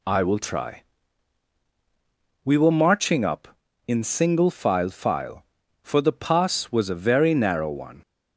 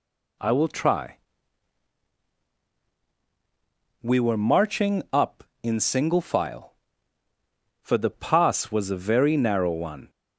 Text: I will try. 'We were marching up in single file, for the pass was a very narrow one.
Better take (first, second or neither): second